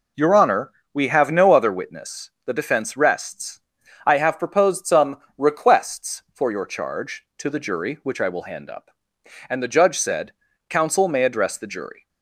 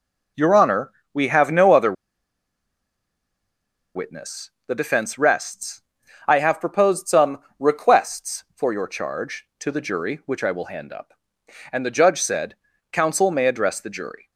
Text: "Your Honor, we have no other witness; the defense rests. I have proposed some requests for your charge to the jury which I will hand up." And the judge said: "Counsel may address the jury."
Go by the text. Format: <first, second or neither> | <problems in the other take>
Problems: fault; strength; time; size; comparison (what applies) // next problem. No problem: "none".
first | pauses between "other" and "witness"; strong; at 1.9 s; 2.0 s long // pauses between "some" and "requests"; slight; at 7.3 s; 0.22 s long; slight in the first